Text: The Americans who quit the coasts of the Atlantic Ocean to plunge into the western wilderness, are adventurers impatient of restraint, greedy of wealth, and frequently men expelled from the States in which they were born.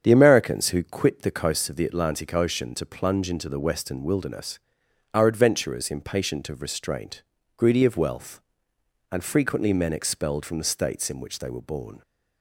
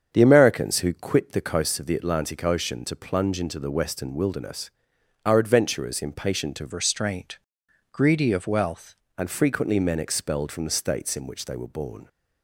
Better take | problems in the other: first | starts louder than the rest; strong; until 1.1 s; 7 dB; strong in the first // changes voice from "restraint" to "wealth"; from 6.7 to 8.9 s; 2.2 s long

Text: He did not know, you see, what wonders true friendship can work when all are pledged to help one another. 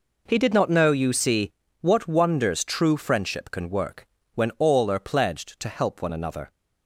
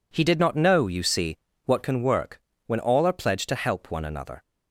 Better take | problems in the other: first | skips "wonders true friendship"; at 1.8 s // pauses between "work" and "when"; slight; at 2.3 s; 0.26 s long; slight in the first

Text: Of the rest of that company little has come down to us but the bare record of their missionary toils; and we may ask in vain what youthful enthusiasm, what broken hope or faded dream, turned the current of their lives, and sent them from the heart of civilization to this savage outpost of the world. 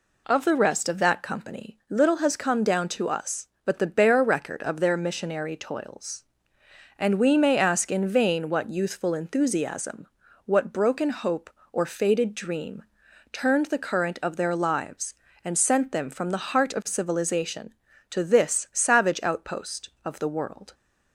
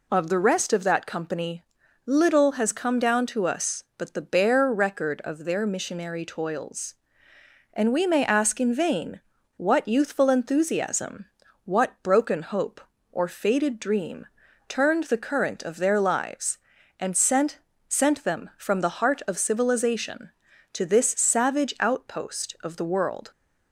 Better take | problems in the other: first | pauses between "company" and "little"; at 1.6 s; 0.42 s long // pauses between "vain" and "what"; at 9.1 s; 0.37 s long // says "sent" twice; at 17.8 s

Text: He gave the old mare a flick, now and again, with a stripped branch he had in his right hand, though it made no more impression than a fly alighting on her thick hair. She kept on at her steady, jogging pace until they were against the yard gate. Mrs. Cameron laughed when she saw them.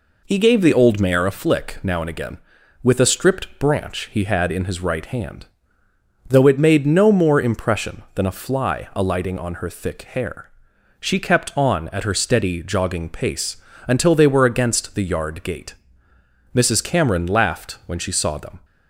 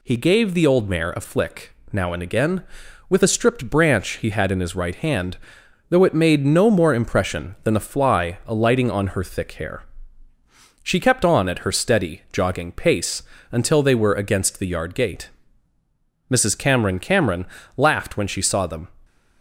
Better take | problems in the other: first | pauses between "pace" and "until"; slight; at 13.2 s; 0.30 s long; slight in the first // says "Cameron" twice; at 16.9 s

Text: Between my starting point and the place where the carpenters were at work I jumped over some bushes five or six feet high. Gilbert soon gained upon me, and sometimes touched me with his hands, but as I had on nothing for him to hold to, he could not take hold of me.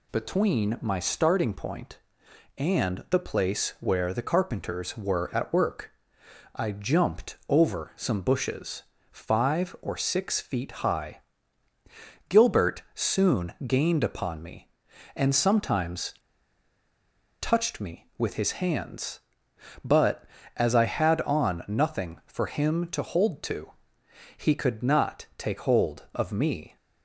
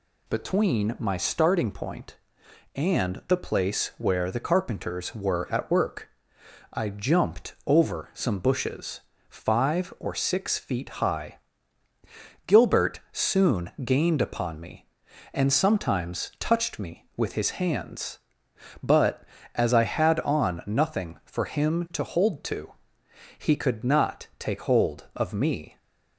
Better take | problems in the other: second | pauses between "work" and "I"; noticeable; at 5.9 s; 0.64 s long; noticeable in the second // pauses between "bushes" and "five"; slight; at 8.8 s; 0.28 s long; slight in the second // pauses between "sometimes" and "touched"; strong; at 16.1 s; 1.2 s long

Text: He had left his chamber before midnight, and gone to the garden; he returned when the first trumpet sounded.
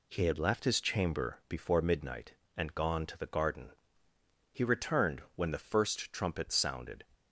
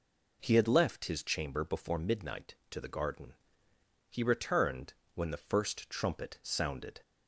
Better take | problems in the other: first | skips "and gone"; at 2.6 s // pauses between "returned" and "when"; slight; at 4.9 s; 0.18 s long

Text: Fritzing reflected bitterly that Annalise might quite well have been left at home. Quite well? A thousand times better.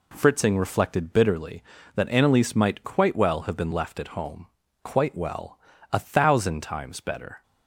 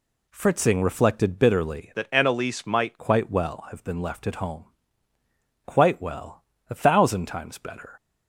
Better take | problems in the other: first | changes voice from "that" to "might"; from 1.9 to 2.9 s; 1.0 s long

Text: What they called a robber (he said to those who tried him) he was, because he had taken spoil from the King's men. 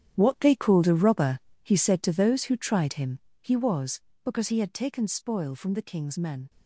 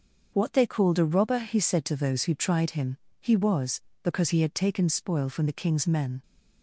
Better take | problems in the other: second | gets quieter; strong; throughout; 11 dB // starts louder than the rest; strong; until 1.1 s; 9.5 dB; also in the second

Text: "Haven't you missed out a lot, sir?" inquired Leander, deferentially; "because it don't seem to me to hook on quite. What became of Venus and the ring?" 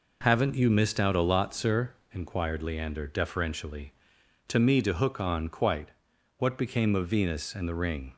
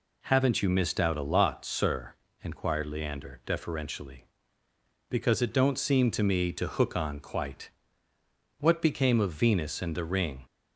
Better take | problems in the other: second | skips "because it don't seem"; at 4.1 s

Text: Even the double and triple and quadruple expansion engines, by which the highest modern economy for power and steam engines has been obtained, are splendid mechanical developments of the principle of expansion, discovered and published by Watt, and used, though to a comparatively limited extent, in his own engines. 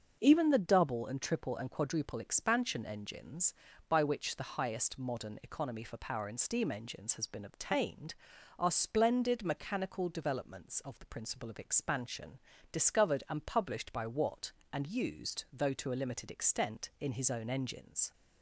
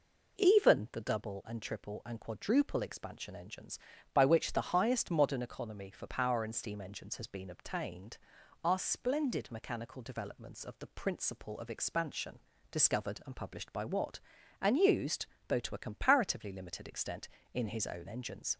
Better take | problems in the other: second | starts louder than the rest; until 1.2 s; 7 dB // skips "comparatively"; at 15.9 s

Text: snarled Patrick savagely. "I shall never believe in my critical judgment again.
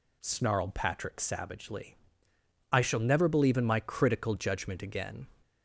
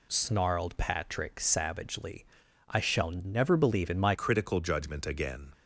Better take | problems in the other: first | changes voice at "critical"; from 4.1 s on; 1.4 s long

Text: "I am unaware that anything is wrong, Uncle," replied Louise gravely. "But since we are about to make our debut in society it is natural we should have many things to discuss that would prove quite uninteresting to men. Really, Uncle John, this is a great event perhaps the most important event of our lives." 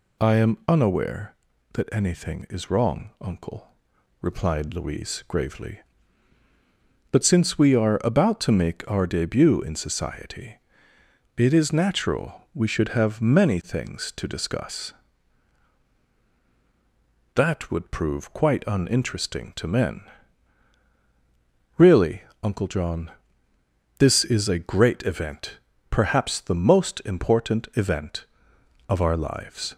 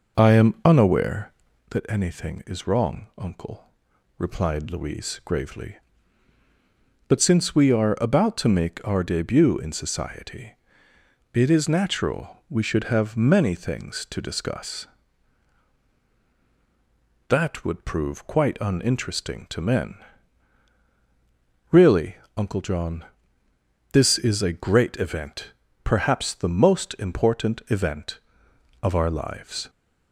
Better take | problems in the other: first | starts louder than the rest; noticeable; until 1.8 s; 5.5 dB // pauses between "society" and "it"; noticeable; at 10.5 s; 0.78 s long; noticeable in the first // pauses between "event" and "perhaps"; slight; at 25.5 s; 0.30 s long; slight in the first

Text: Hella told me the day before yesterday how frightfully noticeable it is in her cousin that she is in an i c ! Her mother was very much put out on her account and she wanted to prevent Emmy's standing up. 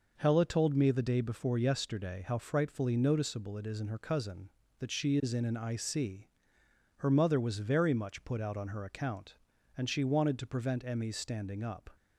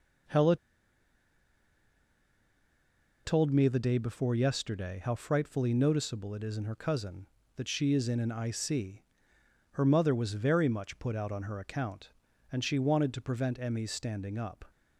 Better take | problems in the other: first | pauses between "Hella" and "told"; strong; at 0.5 s; 2.6 s long

